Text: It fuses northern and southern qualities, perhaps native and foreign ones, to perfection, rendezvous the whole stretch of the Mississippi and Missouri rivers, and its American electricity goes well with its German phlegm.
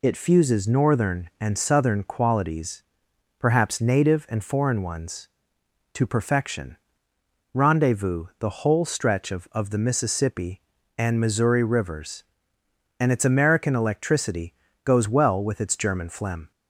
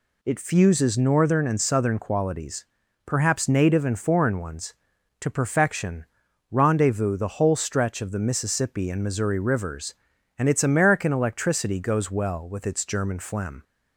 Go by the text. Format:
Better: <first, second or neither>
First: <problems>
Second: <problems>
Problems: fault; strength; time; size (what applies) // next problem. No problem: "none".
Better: second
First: says "of" twice; at 9.5 s // pauses between "electricity" and "goes"; slight; at 14.5 s; 0.32 s long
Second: none